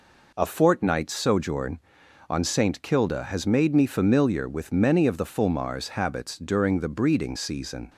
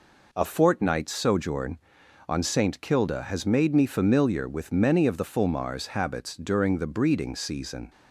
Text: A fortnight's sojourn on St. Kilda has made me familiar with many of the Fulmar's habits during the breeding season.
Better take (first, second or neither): neither